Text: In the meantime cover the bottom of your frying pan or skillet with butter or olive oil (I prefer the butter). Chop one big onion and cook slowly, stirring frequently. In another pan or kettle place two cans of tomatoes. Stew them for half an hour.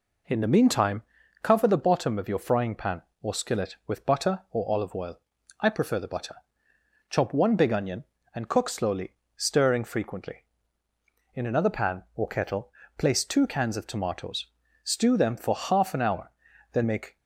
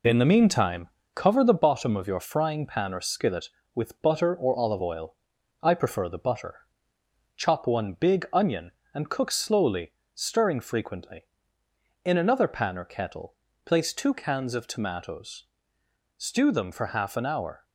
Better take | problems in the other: second | pauses between "meantime" and "cover"; at 1.0 s; 0.40 s long; slight in the second // pauses between "kettle" and "place"; slight; at 12.7 s; 0.28 s long; slight in the second // goes on to say "Then make"; slight; from 16.7 s on; 0.46 s long

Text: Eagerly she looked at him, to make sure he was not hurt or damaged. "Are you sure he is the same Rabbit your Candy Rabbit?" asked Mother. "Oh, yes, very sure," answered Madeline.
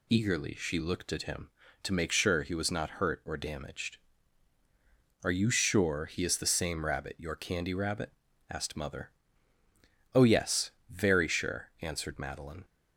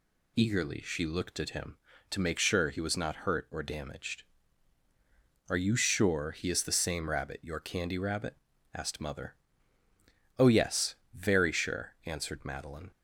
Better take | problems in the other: neither | none

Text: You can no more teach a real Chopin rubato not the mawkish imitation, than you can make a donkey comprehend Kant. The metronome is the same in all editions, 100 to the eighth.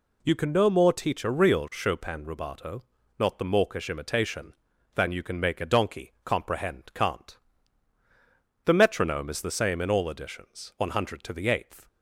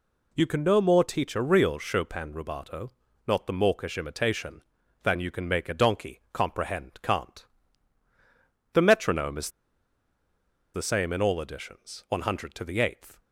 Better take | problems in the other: first | pauses between "rubato" and "not"; slight; at 2.9 s; 0.36 s long; slight in the first // pauses between "is" and "the"; strong; at 9.4 s; 1.2 s long

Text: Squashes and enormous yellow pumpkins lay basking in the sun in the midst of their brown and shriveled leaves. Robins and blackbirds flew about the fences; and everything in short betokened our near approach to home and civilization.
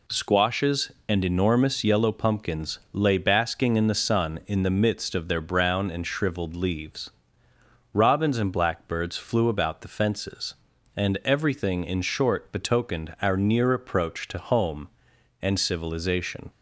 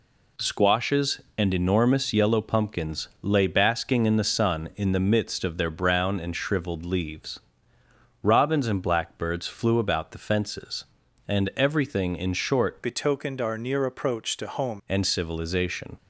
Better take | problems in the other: first | changes voice from "betokened" to "home"; from 12.8 to 14.8 s; 2.0 s long

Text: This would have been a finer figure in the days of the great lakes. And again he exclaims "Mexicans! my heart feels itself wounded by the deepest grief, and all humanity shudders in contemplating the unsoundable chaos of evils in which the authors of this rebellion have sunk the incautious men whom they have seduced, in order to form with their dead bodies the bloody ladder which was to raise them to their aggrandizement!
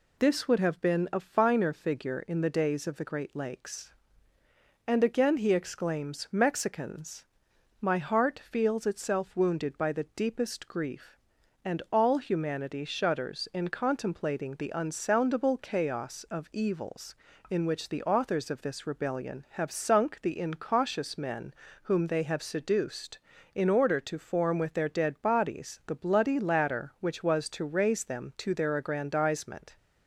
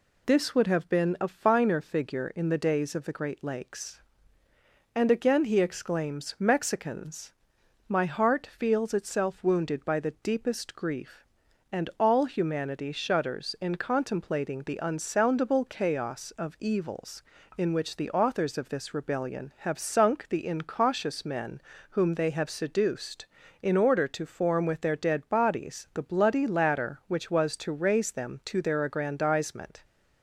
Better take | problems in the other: neither | pauses between "men" and "whom"; slight; the same in both

